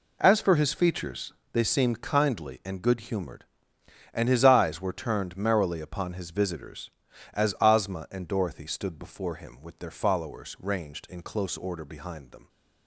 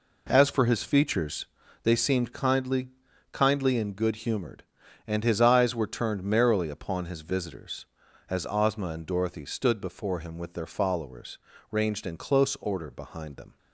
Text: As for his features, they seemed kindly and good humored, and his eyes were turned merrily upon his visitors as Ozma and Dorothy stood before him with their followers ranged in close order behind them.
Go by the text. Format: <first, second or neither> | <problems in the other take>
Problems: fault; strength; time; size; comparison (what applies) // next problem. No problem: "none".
first | says "kindly" twice; at 3.3 s // pauses between "followers" and "ranged"; slight; at 11.3 s; 0.34 s long